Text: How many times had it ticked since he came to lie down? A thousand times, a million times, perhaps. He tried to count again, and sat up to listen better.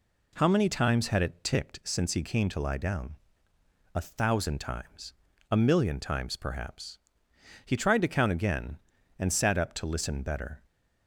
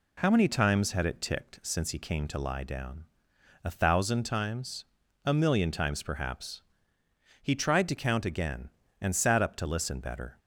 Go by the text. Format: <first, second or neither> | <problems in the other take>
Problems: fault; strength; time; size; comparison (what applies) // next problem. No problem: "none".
neither | none